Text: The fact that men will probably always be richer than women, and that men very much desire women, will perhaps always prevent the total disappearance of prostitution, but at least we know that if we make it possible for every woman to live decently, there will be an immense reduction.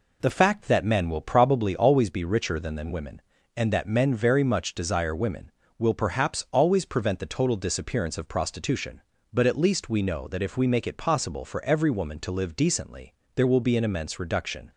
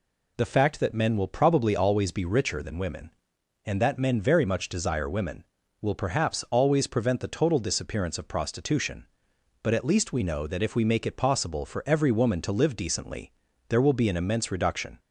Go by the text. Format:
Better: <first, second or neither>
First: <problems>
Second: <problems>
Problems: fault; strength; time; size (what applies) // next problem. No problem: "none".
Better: second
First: says "than" twice; at 2.7 s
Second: none